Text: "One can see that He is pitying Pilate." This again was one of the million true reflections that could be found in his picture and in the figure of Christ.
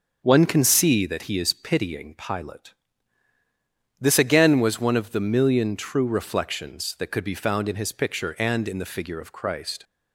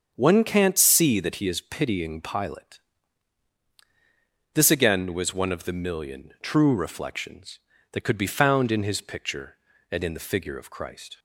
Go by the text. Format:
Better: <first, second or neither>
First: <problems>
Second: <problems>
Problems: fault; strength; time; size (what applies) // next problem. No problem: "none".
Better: first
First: starts louder than the rest; until 1.2 s; 6.5 dB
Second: starts louder than the rest; strong; until 1.1 s; 7.5 dB // says "can't" for "can"; at 0.4 s